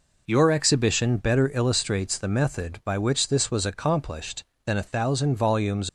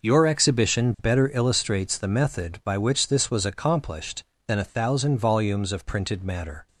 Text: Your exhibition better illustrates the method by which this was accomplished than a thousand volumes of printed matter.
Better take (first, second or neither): second